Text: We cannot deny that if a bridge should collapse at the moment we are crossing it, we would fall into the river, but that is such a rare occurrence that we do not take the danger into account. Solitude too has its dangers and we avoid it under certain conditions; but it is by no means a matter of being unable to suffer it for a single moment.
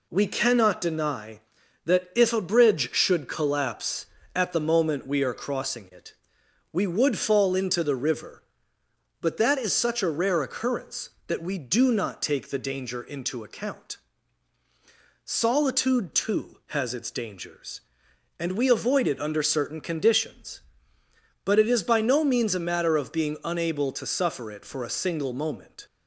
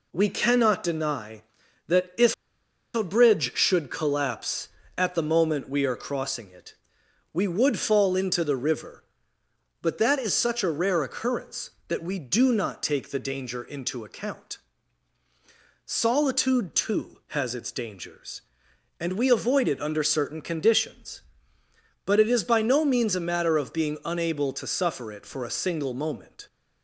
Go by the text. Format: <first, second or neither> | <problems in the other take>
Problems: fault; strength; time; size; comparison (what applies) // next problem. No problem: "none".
first | pauses between "if" and "a"; noticeable; at 2.3 s; 0.60 s long